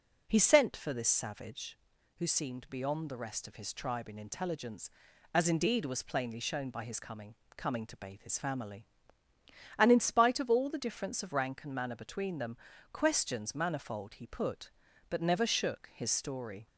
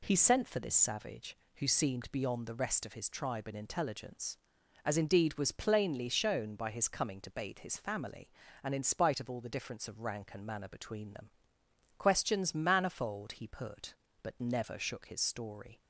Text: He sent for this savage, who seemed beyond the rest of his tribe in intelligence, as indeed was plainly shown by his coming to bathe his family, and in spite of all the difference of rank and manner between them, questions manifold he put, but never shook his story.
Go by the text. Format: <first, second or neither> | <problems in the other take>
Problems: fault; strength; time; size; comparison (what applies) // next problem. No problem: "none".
second | says "coming" twice; at 7.5 s